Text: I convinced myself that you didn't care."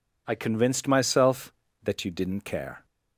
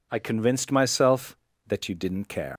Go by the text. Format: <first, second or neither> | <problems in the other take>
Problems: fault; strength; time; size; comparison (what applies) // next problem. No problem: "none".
first | leaves "care" unfinished; at 2.5 s; 130 ms